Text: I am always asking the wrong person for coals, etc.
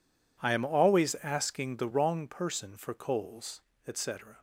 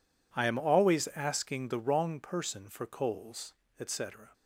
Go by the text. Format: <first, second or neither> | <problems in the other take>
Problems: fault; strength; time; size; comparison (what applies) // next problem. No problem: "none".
neither | none